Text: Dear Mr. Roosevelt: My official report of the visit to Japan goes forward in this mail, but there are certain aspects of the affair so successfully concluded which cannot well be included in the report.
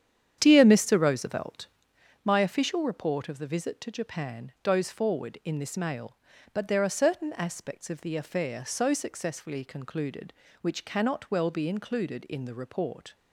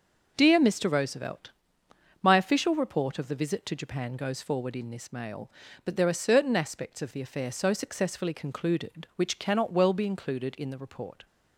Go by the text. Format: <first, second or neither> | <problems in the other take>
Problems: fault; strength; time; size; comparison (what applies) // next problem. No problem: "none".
second | starts louder than the rest; strong; until 2.0 s; 9 dB